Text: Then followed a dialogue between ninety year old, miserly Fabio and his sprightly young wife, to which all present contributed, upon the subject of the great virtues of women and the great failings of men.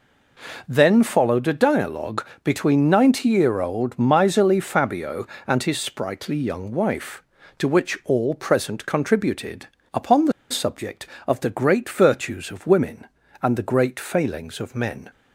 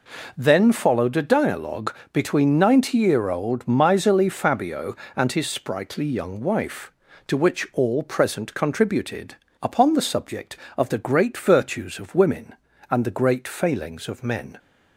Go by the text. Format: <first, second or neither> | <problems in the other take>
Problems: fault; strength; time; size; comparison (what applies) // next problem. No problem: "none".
second | pauses between "dialogue" and "between"; slight; at 2.2 s; 0.20 s long; slight in the second // pauses between "the" and "subject"; slight; at 10.3 s; 0.20 s long